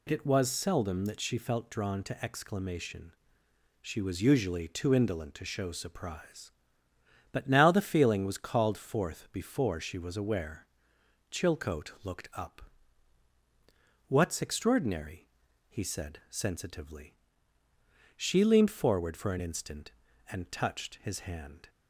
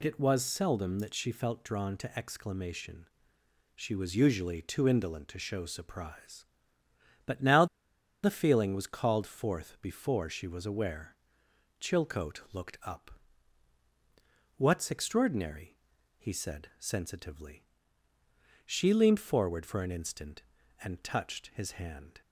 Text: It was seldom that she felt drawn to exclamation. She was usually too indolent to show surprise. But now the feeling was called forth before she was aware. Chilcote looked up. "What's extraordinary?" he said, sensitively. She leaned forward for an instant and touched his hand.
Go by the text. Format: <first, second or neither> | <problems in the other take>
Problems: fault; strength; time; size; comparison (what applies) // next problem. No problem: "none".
first | pauses between "now" and "the"; noticeable; at 7.6 s; 0.57 s long